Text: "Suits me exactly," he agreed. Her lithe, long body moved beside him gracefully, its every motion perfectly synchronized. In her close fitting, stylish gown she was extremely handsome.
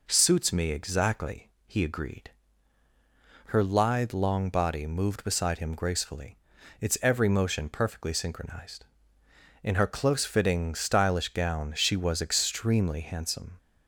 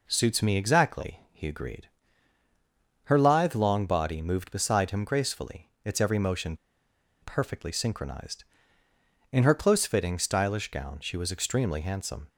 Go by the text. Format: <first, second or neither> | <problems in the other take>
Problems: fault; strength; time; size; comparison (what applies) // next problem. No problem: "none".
first | pauses between "motion" and "perfectly"; noticeable; at 6.5 s; 0.66 s long